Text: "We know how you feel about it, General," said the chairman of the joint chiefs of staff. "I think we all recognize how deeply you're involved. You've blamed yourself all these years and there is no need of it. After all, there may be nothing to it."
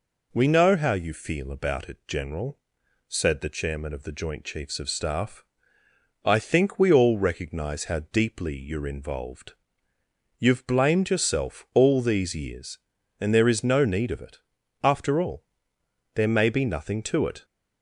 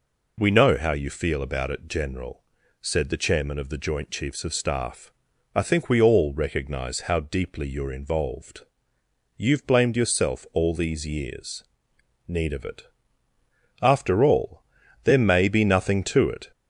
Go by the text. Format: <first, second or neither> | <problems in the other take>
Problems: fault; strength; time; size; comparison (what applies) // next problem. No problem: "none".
first | skips "and there is no"; at 11.9 s